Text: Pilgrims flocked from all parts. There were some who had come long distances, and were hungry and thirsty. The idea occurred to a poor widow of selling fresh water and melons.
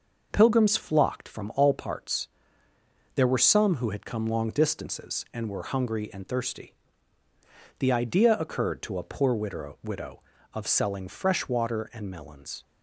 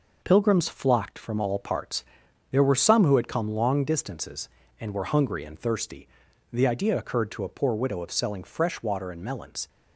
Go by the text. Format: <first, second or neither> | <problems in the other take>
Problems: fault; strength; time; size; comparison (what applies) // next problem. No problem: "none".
second | says "widow" twice; at 9.8 s